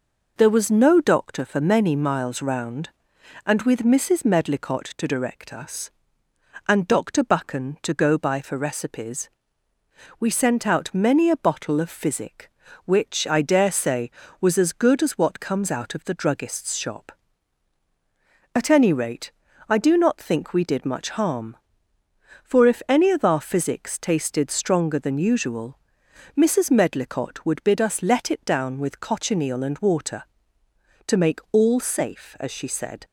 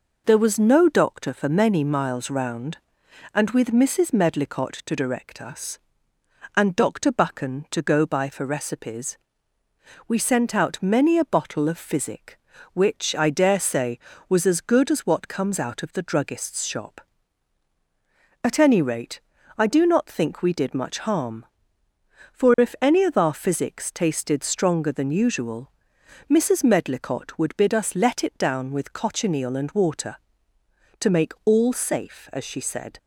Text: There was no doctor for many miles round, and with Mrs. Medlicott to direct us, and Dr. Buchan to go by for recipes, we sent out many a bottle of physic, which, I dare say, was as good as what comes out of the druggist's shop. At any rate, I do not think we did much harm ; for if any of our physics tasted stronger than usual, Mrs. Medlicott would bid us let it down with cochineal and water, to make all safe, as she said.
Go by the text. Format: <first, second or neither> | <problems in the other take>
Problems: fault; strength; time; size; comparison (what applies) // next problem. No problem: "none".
neither | none